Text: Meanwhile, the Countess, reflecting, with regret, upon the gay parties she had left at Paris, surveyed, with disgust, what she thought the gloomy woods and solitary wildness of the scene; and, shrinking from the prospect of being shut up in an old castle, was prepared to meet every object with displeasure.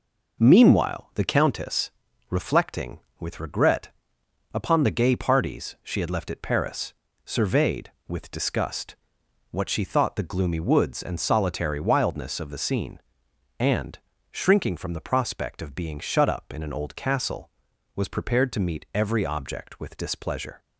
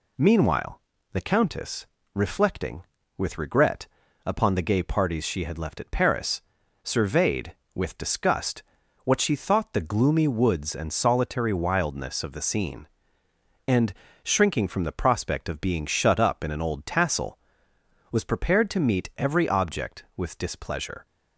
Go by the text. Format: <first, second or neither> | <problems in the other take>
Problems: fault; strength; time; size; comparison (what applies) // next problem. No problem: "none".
first | says "tassel" for "castle"; at 16.8 s